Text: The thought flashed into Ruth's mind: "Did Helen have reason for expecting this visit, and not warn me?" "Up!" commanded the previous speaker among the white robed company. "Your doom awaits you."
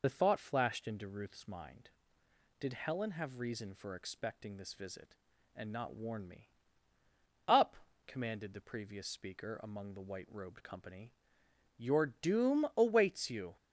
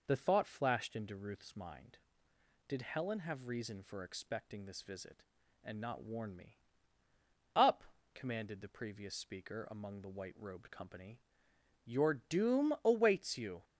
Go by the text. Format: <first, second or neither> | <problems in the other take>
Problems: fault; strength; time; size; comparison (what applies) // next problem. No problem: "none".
second | loses the start of "The"; at 0.0 s; 45 ms